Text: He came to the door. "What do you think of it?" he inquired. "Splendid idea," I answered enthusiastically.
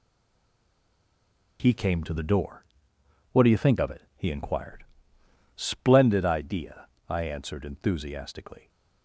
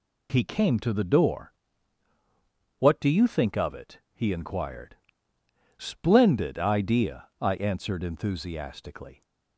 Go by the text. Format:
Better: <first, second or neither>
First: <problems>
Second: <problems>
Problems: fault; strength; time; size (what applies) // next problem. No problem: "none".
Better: second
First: stays silent before the first word; noticeable; until 1.5 s; 1.5 s long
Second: none